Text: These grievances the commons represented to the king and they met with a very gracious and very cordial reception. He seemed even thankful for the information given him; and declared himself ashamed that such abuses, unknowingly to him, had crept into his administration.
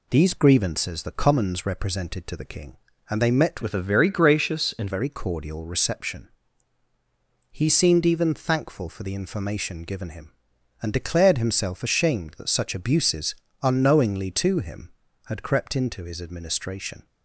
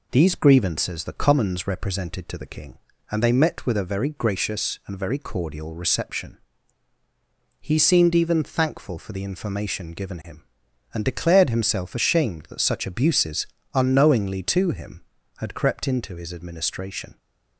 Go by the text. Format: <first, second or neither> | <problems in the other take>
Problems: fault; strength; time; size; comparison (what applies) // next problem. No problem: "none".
second | changes voice from "with" to "and"; from 3.6 to 4.8 s; 1.2 s long